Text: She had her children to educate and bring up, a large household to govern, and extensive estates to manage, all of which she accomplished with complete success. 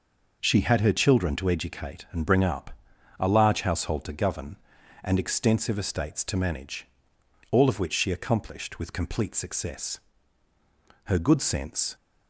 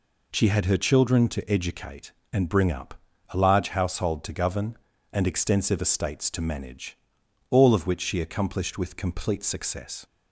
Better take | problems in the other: second | goes on to say "Her good sense"; noticeable; from 11.0 s on; 0.90 s long

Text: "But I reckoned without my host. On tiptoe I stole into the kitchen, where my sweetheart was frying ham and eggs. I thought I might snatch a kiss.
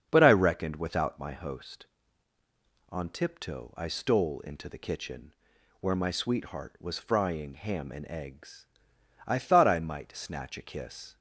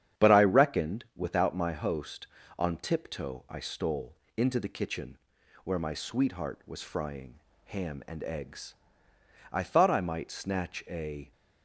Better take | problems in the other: first | starts louder than the rest; strong; until 1.2 s; 9 dB; strong in the first // pauses between "stole" and "into"; slight; at 4.1 s; 0.22 s long // pauses between "frying" and "ham"; slight; at 7.3 s; 0.26 s long // stops before "kiss"; at 11.3 s

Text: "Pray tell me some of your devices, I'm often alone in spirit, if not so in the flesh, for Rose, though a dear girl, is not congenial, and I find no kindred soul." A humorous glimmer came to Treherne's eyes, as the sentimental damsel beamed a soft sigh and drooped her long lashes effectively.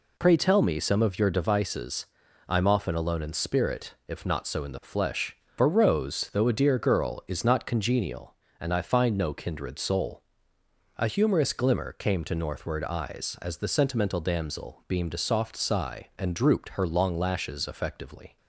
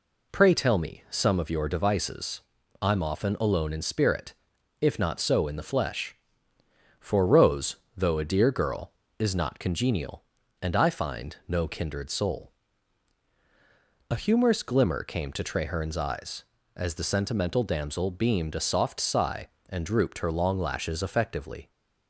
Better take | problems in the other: second | says "Northward" for "Treherne's"; at 12.3 s

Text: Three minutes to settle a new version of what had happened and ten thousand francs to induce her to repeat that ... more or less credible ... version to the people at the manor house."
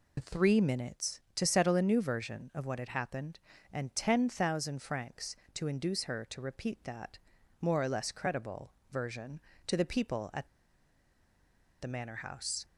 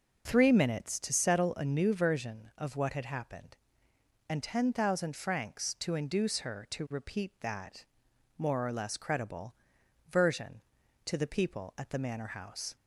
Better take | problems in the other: second | pauses between "at" and "the"; strong; at 10.4 s; 1.3 s long

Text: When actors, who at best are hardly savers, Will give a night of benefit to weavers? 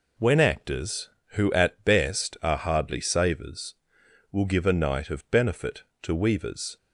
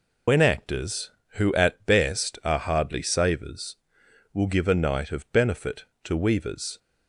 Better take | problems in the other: first | loses the start of "When"; at 0.2 s; 75 ms

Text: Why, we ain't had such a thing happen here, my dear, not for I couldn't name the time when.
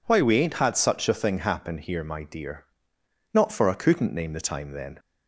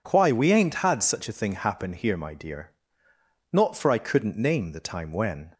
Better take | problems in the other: second | says "then" for "when"; at 4.7 s

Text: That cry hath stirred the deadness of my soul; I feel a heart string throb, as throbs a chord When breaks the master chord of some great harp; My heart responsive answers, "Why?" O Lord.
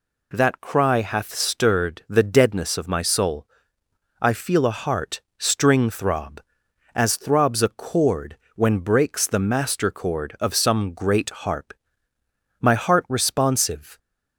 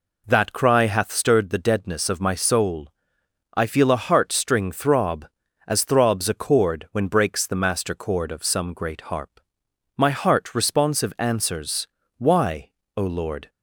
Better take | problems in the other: second | pauses between "heart" and "string"; slight; at 5.1 s; 0.18 s long // pauses between "chord" and "When"; slight; at 8.3 s; 0.18 s long // stops before "answers Why O Lord"; at 13.9 s

